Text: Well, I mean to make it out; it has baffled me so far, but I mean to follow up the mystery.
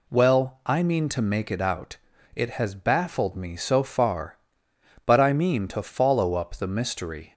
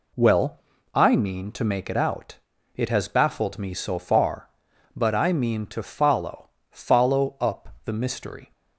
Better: first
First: none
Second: says "follow" twice; at 6.6 s

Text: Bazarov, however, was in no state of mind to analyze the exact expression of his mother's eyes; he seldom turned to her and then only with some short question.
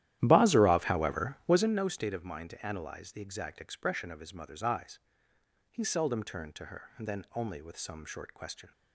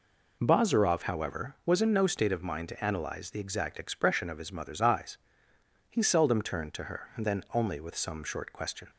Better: second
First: starts louder than the rest; strong; until 1.8 s; 12.5 dB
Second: none

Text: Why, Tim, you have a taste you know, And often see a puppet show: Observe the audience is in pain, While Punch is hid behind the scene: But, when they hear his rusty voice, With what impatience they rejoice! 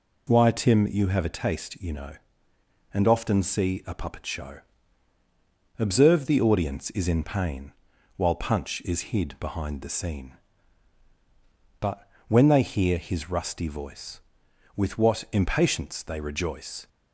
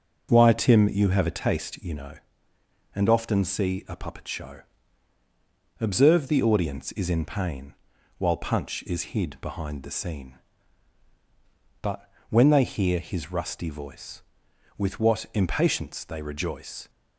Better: first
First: none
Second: starts louder than the rest; noticeable; until 2.1 s; 5.5 dB

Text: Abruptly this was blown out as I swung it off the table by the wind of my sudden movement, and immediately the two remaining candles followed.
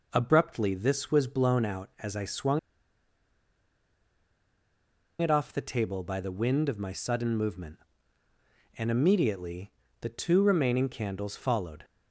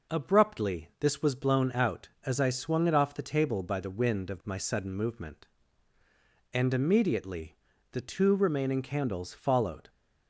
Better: second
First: pauses between "swung" and "it"; strong; at 2.5 s; 2.6 s long // pauses between "immediately" and "the"; slight; at 9.7 s; 0.32 s long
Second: pauses between "immediately" and "the"; slight; at 7.5 s; 0.34 s long

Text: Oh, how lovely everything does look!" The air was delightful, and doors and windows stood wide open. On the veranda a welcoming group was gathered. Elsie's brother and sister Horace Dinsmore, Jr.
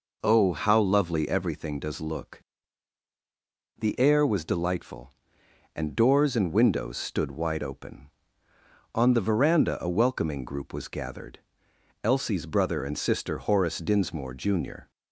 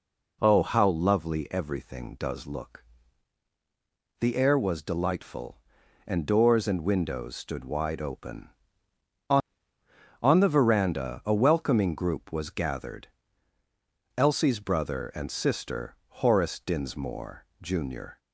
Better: first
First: none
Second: says "On" twice; at 10.2 s

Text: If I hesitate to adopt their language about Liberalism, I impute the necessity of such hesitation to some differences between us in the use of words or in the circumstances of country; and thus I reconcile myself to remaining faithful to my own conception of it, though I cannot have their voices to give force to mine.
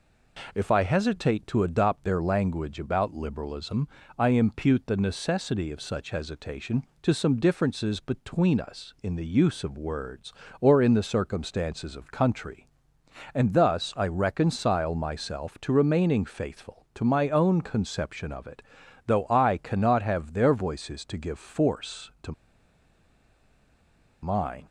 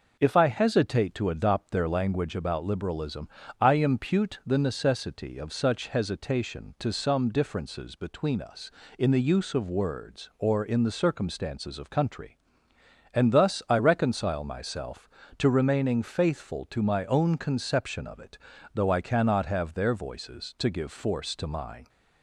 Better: second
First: pauses between "to" and "mine"; strong; at 22.3 s; 1.9 s long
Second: none

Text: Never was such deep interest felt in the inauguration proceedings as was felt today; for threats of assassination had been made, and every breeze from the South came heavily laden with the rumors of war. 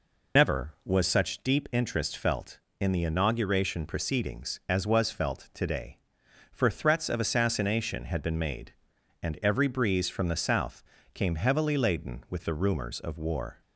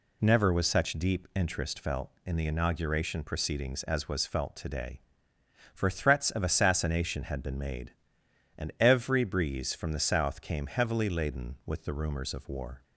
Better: second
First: loses the start of "Never"; at 0.3 s; 100 ms // pauses between "South" and "came"; slight; at 10.8 s; 0.32 s long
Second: none

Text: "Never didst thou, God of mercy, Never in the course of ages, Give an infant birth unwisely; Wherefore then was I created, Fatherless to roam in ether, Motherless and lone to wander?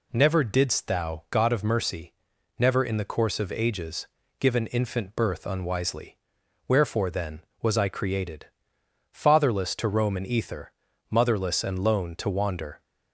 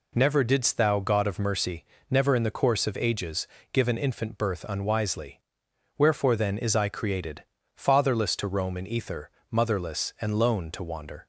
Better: first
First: none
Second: says "is" for "was"; at 6.5 s

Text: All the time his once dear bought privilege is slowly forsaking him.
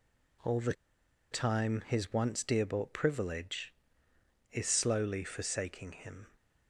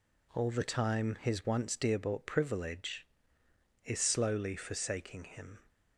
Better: second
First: pauses between "the" and "time"; noticeable; at 0.7 s; 0.58 s long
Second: none

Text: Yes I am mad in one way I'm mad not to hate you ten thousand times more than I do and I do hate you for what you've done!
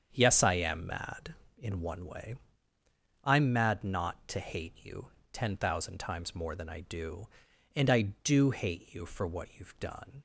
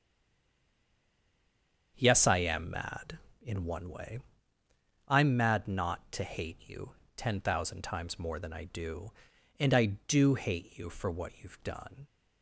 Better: first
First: starts louder than the rest; strong; until 1.1 s; 7.5 dB // pauses between "way" and "I'm"; noticeable; at 2.3 s; 0.88 s long // pauses between "you" and "ten"; slight; at 5.0 s; 0.24 s long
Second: stays silent before the first word; noticeable; until 1.9 s; 1.9 s long // starts louder than the rest; strong; until 2.9 s; 7.5 dB // pauses between "way" and "I'm"; noticeable; at 4.1 s; 0.88 s long // pauses between "you" and "ten"; slight; at 6.9 s; 0.24 s long

